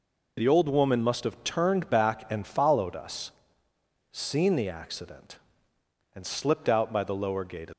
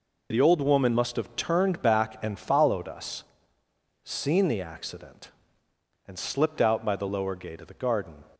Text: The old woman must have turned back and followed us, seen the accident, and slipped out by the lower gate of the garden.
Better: second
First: stops before "of the garden"; at 7.7 s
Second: none

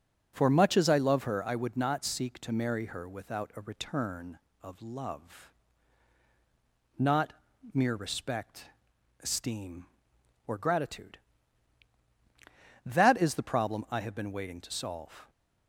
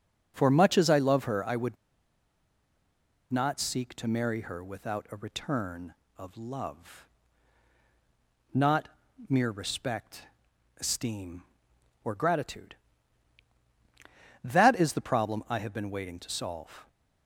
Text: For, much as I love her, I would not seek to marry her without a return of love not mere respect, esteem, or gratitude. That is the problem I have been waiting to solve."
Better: first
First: pauses between "love" and "not"; strong; at 5.5 s; 1.4 s long // pauses between "not" and "mere"; at 7.3 s; 0.40 s long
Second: pauses between "would" and "not"; strong; at 1.7 s; 1.5 s long // pauses between "love" and "not"; strong; at 7.0 s; 1.4 s long // pauses between "not" and "mere"; at 8.8 s; 0.40 s long

